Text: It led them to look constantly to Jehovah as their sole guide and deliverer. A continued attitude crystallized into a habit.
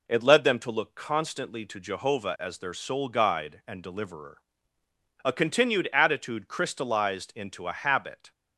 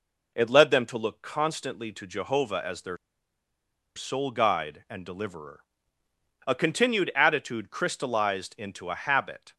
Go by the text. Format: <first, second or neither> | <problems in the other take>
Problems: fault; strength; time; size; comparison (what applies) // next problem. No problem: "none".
first | pauses between "their" and "sole"; at 2.9 s; 0.98 s long